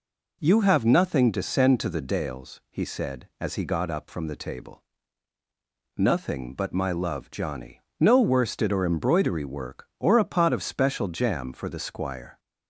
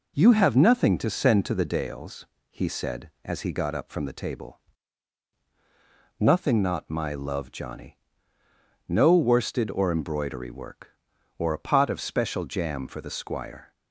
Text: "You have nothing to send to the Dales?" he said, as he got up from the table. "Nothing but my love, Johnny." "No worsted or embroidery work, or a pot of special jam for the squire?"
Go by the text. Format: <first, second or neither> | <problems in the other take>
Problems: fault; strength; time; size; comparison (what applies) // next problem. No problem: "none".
first | says "not" for "but"; at 6.6 s